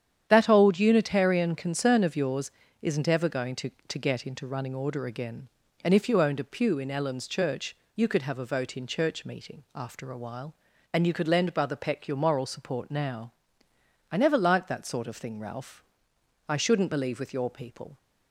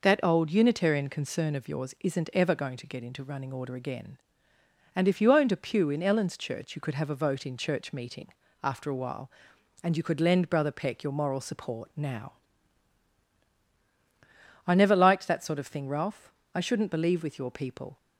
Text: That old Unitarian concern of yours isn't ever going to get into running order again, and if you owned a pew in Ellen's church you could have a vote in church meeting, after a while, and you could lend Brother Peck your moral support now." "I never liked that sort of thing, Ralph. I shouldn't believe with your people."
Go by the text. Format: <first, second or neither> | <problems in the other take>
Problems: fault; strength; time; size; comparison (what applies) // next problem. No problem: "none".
second | starts louder than the rest; strong; until 1.3 s; 9.5 dB // pauses between "yours" and "isn't"; slight; at 2.4 s; 0.32 s long // says "to" twice; at 3.7 s // pauses between "church" and "you"; slight; at 7.7 s; 0.22 s long